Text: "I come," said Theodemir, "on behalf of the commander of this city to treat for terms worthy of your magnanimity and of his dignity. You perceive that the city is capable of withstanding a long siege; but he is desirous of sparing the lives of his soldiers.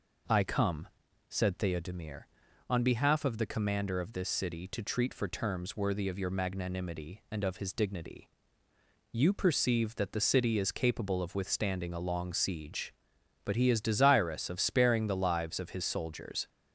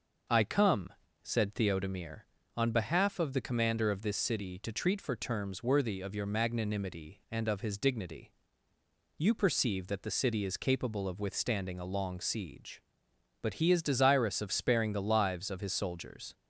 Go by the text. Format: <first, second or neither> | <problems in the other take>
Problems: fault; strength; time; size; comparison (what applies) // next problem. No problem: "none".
neither | none